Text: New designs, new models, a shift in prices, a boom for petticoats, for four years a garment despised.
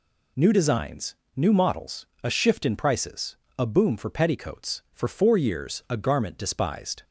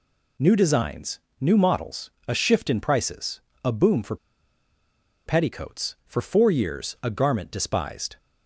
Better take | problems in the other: first | pauses between "for" and "petticoats"; at 4.1 s; 1.1 s long

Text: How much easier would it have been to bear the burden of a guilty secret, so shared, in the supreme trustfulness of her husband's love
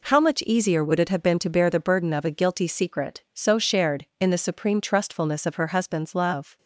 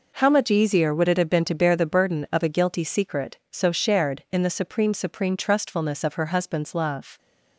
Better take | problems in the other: first | says "supreme" twice; at 4.9 s

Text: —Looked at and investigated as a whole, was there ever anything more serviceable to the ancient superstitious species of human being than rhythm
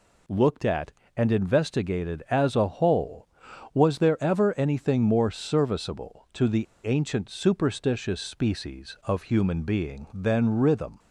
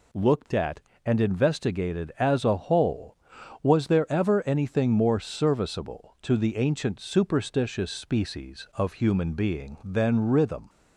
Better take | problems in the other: second | pauses between "the" and "ancient"; slight; at 6.6 s; 0.21 s long

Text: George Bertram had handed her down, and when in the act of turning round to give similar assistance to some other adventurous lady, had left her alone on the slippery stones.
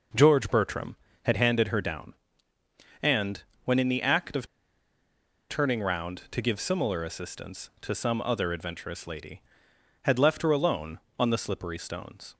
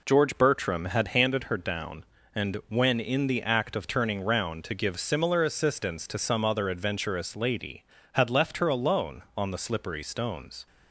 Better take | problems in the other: second | pauses between "and" and "when"; slight; at 3.4 s; 0.22 s long // pauses between "of" and "turning"; at 4.4 s; 1.0 s long

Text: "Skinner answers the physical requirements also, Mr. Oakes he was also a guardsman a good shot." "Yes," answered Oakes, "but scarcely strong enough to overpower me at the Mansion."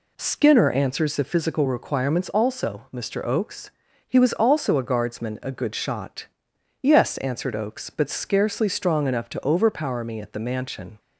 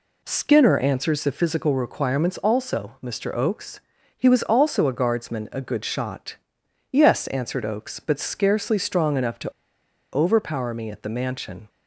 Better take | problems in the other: first | pauses between "Oakes" and "he"; slight; at 3.8 s; 0.36 s long; slight in the first // pauses between "to" and "overpower"; noticeable; at 9.5 s; 0.60 s long

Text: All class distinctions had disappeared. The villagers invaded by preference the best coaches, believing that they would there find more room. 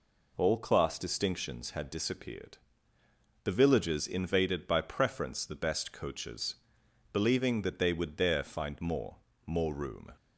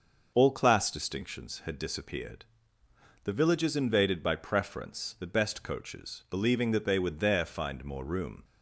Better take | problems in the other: second | says "more" twice; at 9.4 s

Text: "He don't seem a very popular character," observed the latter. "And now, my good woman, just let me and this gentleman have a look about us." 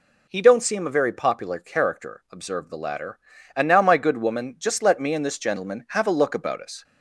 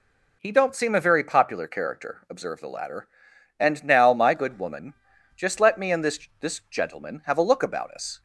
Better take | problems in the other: first | says "this" twice; at 6.3 s

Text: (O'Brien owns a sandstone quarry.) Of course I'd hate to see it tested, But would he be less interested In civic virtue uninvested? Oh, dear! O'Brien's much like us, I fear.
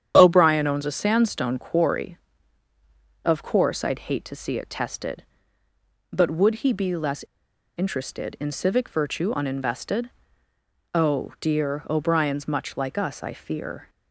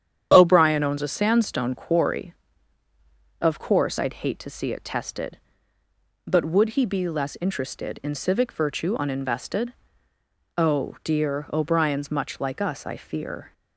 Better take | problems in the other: second | starts louder than the rest; strong; until 1.1 s; 9.5 dB; strong in the second // pauses between "less" and "interested"; noticeable; at 7.2 s; 0.55 s long

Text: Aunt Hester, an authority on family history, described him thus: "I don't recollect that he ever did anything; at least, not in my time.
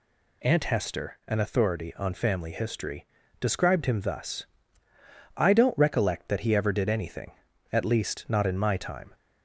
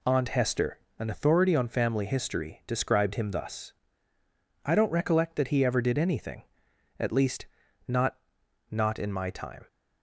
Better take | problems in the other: first | says "not" twice; at 8.7 s

